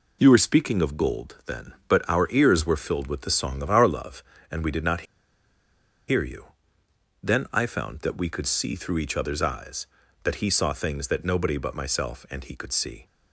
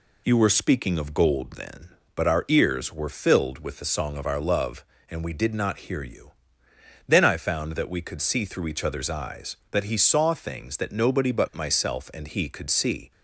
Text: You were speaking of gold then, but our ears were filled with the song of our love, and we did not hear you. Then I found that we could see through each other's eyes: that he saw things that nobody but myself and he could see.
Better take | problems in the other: second | pauses between "not" and "hear"; at 5.0 s; 1.0 s long

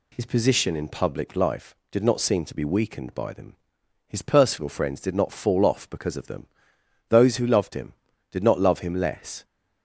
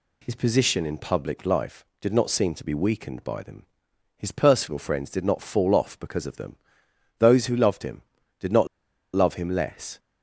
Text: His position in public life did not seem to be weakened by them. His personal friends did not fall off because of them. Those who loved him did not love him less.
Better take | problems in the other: first | pauses between "not" and "love"; noticeable; at 8.6 s; 0.47 s long

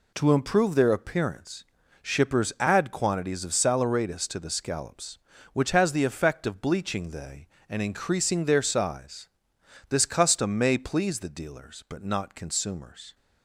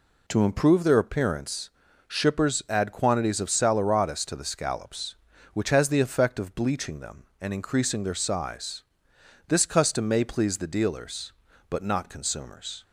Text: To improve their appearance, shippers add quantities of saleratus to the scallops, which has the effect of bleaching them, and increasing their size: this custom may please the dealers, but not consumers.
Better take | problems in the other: second | says "they" for "them"; at 7.0 s

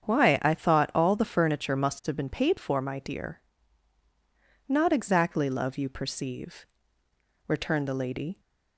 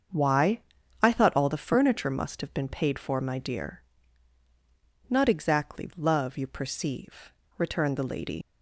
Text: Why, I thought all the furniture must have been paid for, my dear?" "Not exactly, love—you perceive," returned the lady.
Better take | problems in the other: first | starts louder than the rest; until 1.5 s; 7 dB; strong in the first // leaves "lady" unfinished; at 8.4 s; 90 ms

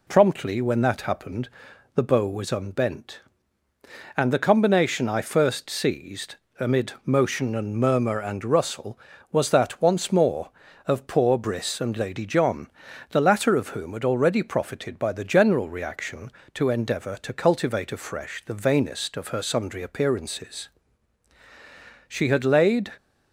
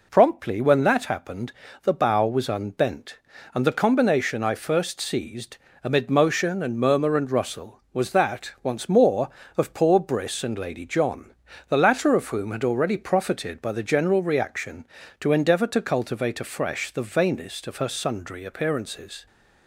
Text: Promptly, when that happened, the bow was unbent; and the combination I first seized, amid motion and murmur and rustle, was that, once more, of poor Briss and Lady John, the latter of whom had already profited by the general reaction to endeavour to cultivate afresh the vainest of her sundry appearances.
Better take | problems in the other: second | goes on to say "She had laid"; noticeable; from 22.0 s on; 0.86 s long

